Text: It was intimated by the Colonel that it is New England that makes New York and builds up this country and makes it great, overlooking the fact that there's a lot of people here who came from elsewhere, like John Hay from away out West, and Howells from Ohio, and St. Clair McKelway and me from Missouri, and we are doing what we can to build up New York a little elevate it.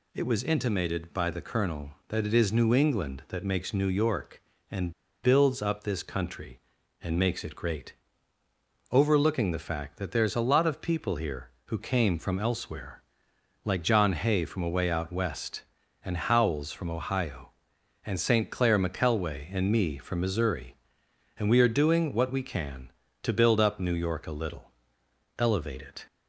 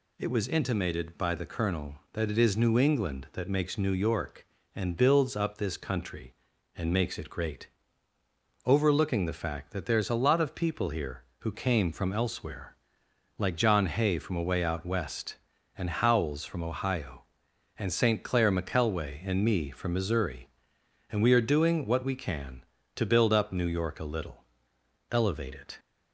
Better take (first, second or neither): second